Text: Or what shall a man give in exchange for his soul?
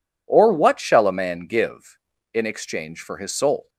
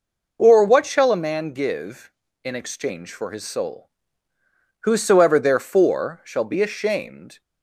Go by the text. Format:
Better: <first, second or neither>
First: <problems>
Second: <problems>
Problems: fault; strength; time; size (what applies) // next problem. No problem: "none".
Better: first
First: none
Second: goes on to say "Whosoever therefore shall be ashamed"; strong; from 4.8 s on; 2.5 s long